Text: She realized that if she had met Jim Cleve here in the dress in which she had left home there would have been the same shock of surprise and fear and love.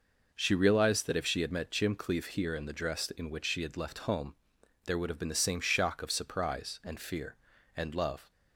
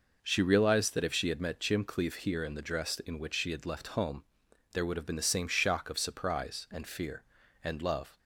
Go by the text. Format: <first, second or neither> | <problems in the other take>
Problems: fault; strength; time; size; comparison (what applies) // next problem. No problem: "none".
neither | pauses between "home" and "there"; noticeable; the same in both